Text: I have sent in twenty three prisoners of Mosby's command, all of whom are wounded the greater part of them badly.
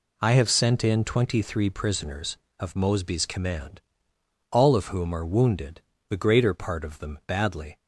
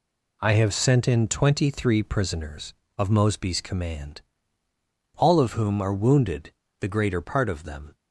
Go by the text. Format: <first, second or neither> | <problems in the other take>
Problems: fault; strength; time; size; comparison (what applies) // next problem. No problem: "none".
first | pauses between "wounded" and "the"; slight; at 6.5 s; 0.26 s long; slight in the first // stops before "badly"; at 7.9 s